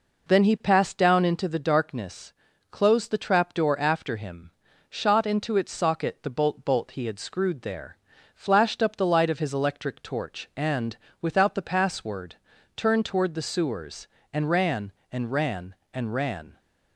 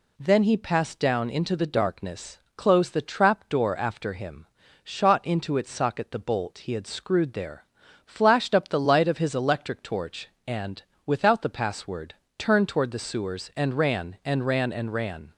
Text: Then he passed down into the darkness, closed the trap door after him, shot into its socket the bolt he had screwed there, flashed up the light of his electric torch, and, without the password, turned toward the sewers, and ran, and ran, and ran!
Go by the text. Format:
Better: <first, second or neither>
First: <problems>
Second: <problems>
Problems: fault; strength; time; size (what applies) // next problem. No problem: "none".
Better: second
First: says "bolt" twice; at 6.6 s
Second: none